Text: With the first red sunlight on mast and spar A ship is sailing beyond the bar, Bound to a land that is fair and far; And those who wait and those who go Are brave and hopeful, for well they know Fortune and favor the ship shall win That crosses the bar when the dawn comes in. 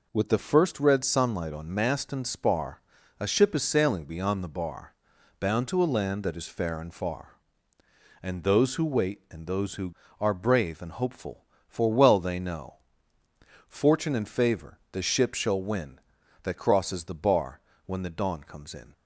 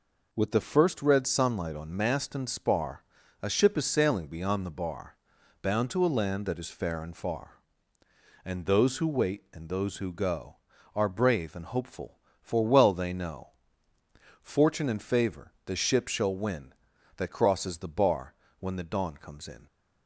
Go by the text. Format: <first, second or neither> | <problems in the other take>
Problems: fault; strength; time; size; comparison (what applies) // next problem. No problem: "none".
second | pauses between "spar" and "A"; at 2.8 s; 0.38 s long; also in the second // skips "go"; at 10.0 s // pauses between "know" and "Fortune"; noticeable; at 12.7 s; 0.92 s long; noticeable in the second // pauses between "bar" and "when"; slight; at 17.5 s; 0.28 s long; slight in the second